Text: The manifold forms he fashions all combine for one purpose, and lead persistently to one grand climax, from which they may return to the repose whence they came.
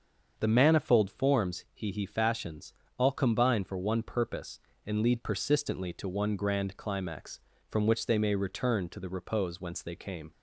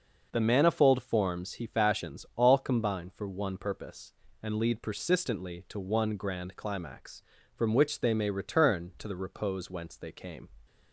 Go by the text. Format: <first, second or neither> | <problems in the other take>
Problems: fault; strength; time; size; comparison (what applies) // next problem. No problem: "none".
second | starts louder than the rest; until 1.3 s; 7 dB // says "he" twice; at 1.9 s // pauses between "fashions" and "all"; slight; at 2.7 s; 0.26 s long